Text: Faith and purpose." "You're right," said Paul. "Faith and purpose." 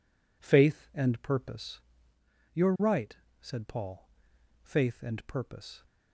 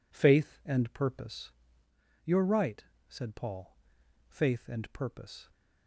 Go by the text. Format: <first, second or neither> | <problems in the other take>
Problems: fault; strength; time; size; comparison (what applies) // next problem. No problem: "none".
neither | none